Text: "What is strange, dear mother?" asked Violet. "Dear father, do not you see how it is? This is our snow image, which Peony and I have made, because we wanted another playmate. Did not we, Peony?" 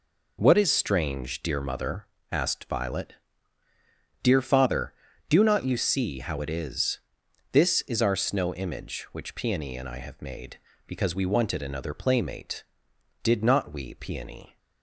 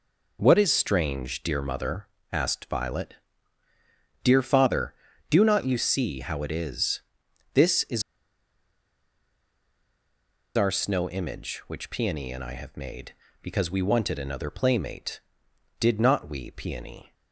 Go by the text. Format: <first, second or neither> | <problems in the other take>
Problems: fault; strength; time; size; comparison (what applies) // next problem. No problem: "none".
first | pauses between "is" and "our"; strong; at 8.0 s; 2.5 s long